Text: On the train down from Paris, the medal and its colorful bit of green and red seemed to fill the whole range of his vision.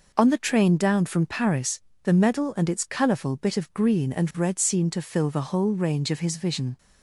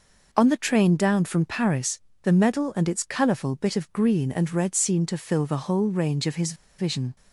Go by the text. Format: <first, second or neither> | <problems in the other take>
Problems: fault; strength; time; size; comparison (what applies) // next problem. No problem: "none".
first | pauses between "his" and "vision"; slight; at 6.5 s; 0.24 s long